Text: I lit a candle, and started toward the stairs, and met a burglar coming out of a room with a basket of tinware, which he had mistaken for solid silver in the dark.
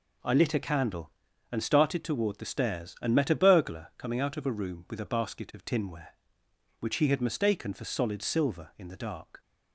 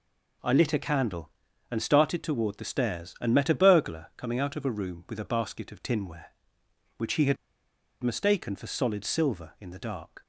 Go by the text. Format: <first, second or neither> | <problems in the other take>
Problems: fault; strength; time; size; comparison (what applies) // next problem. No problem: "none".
first | pauses between "had" and "mistaken"; noticeable; at 7.3 s; 0.67 s long